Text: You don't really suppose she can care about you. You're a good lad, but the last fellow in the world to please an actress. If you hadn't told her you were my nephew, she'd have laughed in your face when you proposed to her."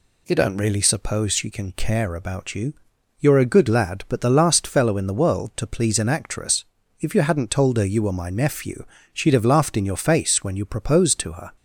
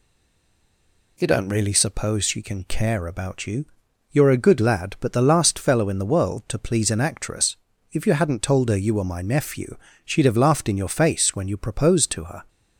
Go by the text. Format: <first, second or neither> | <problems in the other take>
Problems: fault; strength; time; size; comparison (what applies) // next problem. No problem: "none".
first | stays silent before the first word; noticeable; until 1.1 s; 1.1 s long